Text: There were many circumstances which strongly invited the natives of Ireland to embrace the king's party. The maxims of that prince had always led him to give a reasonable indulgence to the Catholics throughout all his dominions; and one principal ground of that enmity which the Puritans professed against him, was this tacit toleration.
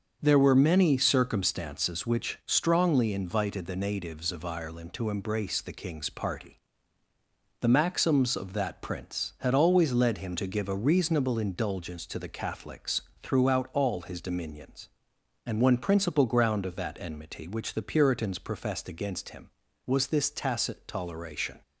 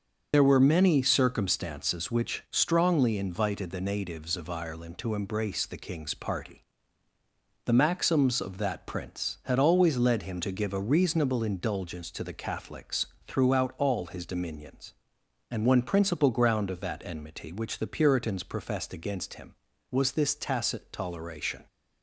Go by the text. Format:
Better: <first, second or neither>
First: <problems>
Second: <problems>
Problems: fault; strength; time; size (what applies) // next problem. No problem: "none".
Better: first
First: starts louder than the rest; until 1.2 s; 7 dB // pauses between "Catholics" and "throughout"; slight; at 13.0 s; 0.22 s long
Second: loses the start of "There"; at 0.3 s; 80 ms // starts louder than the rest; until 1.3 s; 6.5 dB // pauses between "Catholics" and "throughout"; slight; at 13.0 s; 0.22 s long